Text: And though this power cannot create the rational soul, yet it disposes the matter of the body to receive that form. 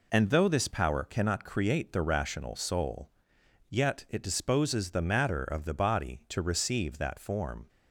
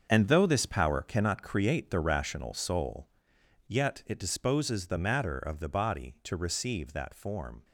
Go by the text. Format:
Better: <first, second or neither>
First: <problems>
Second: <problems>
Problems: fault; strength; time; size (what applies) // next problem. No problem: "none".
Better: first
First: none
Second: gets quieter; strong; throughout; 10.5 dB